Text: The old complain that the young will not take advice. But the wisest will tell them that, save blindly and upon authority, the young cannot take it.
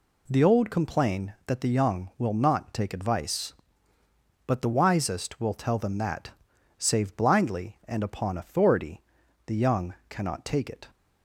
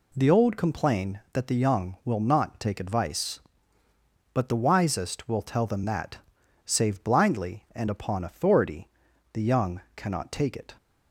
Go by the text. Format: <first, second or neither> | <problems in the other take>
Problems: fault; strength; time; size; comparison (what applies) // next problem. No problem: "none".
neither | pauses between "young" and "cannot"; slight; the same in both